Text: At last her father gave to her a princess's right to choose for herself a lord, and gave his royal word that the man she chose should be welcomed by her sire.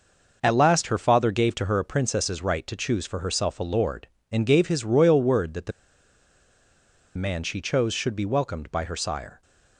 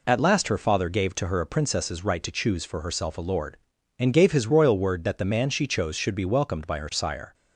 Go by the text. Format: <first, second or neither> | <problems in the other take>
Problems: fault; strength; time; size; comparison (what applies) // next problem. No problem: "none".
second | pauses between "the" and "man"; strong; at 5.7 s; 1.4 s long